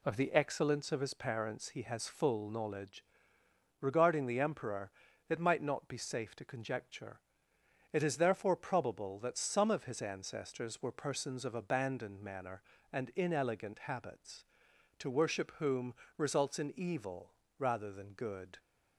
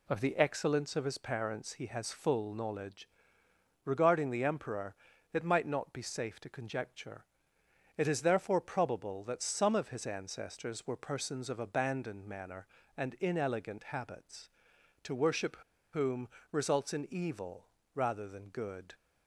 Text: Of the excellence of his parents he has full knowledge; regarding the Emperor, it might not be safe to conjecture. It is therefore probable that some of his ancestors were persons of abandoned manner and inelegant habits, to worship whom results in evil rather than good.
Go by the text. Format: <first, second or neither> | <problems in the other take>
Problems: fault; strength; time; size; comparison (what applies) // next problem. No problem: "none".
first | pauses between "worship" and "whom"; slight; at 15.5 s; 0.35 s long // pauses between "whom" and "results"; slight; at 16.2 s; 0.22 s long; slight in the first // pauses between "evil" and "rather"; slight; at 17.6 s; 0.28 s long; slight in the first